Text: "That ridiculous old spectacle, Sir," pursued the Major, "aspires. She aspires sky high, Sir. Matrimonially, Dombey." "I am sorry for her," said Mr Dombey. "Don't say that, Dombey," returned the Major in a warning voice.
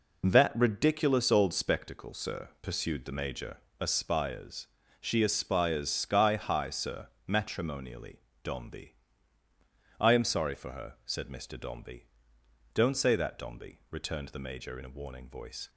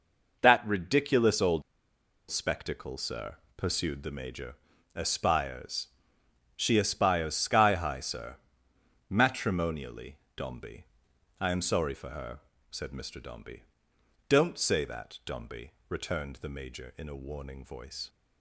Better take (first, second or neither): first